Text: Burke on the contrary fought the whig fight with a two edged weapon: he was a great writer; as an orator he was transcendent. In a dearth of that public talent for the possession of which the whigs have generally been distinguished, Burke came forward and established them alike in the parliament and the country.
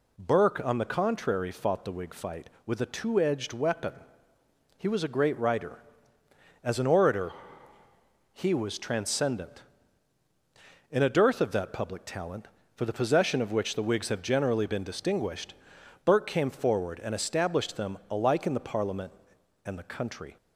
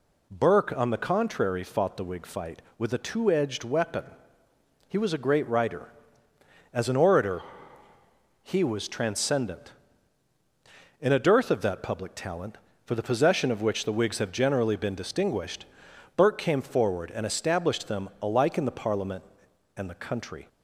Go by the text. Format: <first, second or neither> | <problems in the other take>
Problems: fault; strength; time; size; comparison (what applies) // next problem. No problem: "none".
neither | pauses between "orator" and "he"; the same in both